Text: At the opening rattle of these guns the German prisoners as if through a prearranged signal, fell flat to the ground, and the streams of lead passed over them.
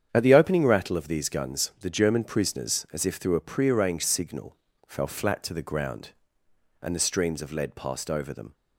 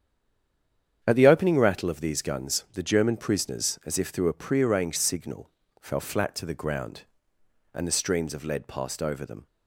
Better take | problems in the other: first | stays silent before the first word; until 1.0 s; 1.0 s long // starts louder than the rest; strong; until 2.0 s; 8.5 dB; strong in the first

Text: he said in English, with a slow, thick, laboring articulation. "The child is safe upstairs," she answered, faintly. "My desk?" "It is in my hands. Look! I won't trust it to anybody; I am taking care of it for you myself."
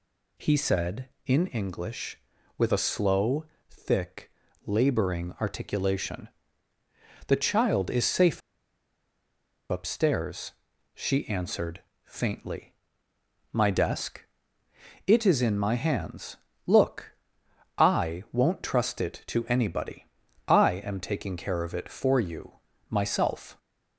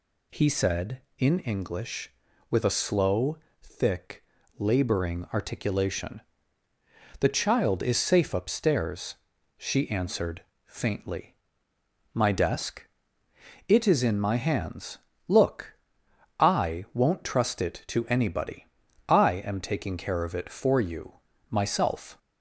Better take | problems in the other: second | pauses between "safe" and "upstairs"; strong; at 8.4 s; 1.2 s long // pauses between "you" and "myself"; slight; at 22.5 s; 0.36 s long; slight in the second

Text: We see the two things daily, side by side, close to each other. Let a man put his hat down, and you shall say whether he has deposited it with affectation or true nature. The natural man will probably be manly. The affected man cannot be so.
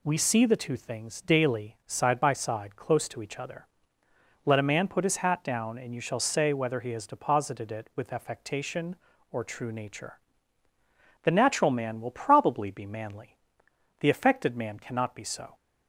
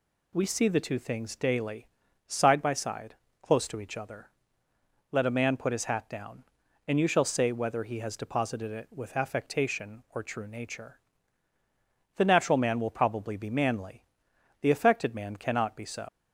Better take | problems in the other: first | leaves "so" unfinished; at 16.0 s; 90 ms

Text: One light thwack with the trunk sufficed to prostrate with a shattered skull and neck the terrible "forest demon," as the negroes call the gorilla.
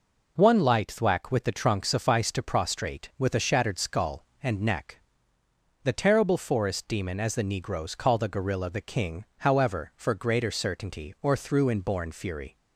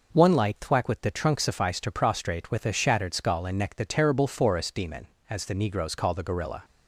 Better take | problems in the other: second | pauses between "neck" and "the"; noticeable; at 4.9 s; 0.84 s long // goes on to say "The King however for greater certainty or through inborn fury"; strong; from 8.6 s on; 3.8 s long

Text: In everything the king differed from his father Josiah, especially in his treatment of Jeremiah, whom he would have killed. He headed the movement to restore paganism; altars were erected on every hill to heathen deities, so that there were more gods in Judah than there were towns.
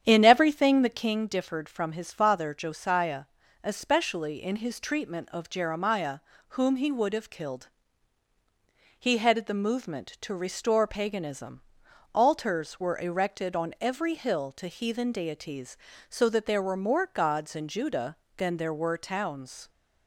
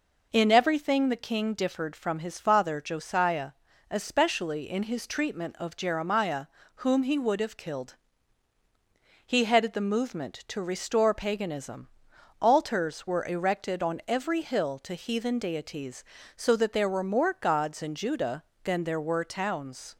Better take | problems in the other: second | starts louder than the rest; strong; until 1.2 s; 9 dB

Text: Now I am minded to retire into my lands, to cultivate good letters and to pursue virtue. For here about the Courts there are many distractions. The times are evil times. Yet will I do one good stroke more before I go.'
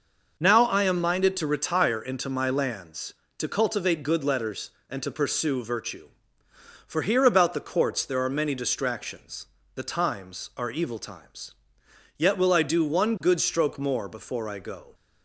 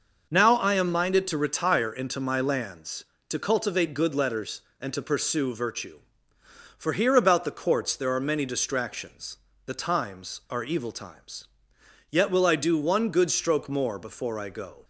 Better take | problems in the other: neither | starts louder than the rest; noticeable; the same in both

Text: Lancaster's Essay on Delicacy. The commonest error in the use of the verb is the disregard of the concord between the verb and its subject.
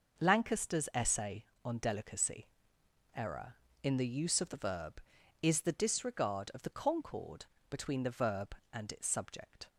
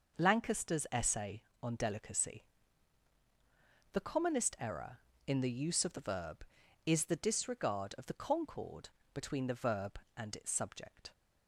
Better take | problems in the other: second | starts louder than the rest; noticeable; until 1.2 s; 6 dB // skips "The commonest"; at 2.8 s // pauses between "concord" and "between"; slight; at 7.4 s; 0.26 s long; slight in the second

